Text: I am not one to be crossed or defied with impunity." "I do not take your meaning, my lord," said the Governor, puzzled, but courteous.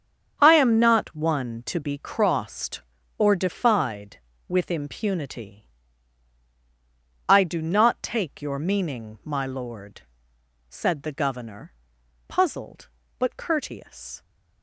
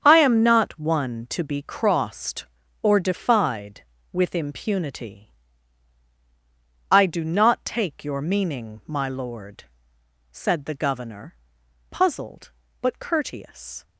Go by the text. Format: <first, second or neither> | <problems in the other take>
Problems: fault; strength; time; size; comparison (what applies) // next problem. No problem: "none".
neither | starts louder than the rest; strong; the same in both